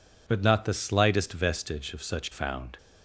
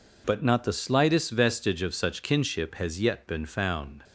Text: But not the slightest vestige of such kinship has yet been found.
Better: second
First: skips "kinship has yet been"; at 2.3 s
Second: none

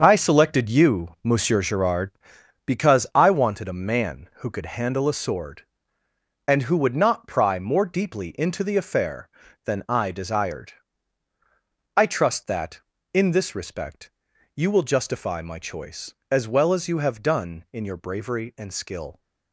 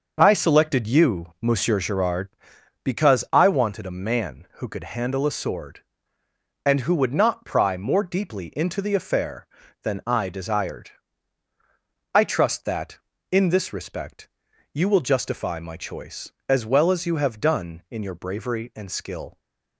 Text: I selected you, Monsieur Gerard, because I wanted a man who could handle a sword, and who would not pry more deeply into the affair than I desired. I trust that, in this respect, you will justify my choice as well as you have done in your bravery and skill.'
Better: second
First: gets quieter; strong; throughout; 10.5 dB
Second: none

